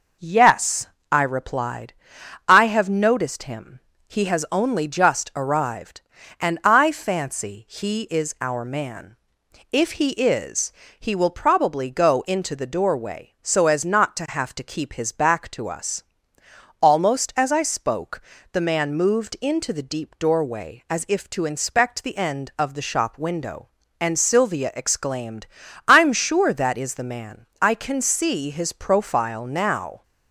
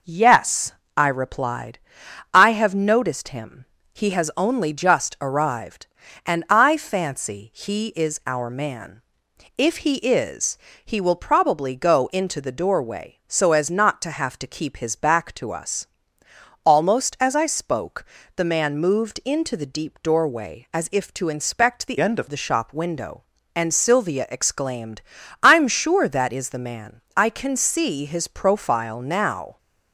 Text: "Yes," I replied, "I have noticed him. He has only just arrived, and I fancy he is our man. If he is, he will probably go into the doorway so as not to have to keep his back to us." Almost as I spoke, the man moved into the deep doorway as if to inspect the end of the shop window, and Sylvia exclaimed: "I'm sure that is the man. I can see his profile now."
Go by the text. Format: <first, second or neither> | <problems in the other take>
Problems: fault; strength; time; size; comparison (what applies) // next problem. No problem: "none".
first | changes voice from "end" to "of"; from 22.0 to 22.2 s; 0.2 s long